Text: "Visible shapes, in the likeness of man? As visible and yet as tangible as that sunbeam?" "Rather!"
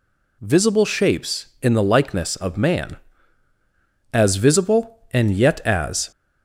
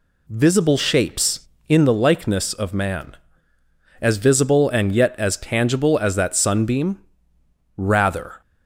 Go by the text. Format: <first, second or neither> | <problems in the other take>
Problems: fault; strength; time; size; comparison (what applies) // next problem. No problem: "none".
second | stops before "tangible as that sunbeam Rather"; at 6.1 s